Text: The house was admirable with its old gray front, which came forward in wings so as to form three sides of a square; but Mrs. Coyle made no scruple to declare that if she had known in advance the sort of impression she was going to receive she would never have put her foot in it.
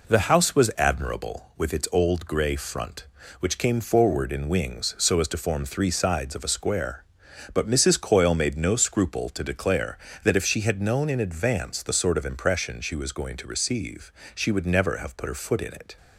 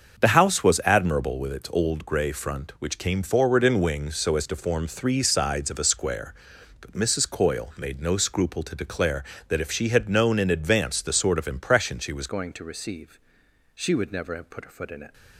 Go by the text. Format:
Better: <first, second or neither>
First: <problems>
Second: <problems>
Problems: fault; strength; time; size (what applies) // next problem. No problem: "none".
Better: first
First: pauses between "receive" and "she"; slight; at 14.1 s; 0.24 s long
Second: starts louder than the rest; until 1.2 s; 7 dB // changes voice at "going"; from 12.2 s on; 2.9 s long // pauses between "receive" and "she"; noticeable; at 13.1 s; 0.56 s long